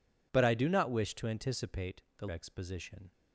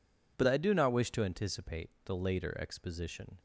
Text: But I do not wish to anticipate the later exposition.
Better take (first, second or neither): second